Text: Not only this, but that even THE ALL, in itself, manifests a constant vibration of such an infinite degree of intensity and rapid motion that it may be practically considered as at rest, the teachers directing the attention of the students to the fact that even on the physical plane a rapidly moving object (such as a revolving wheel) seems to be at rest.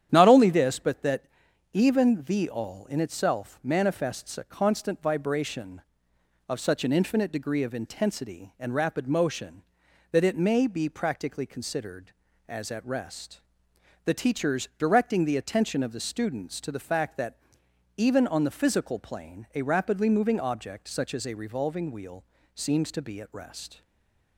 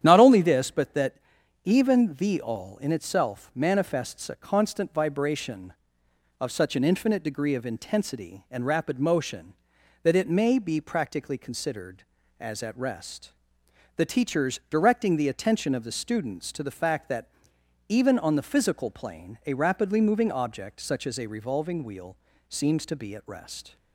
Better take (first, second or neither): second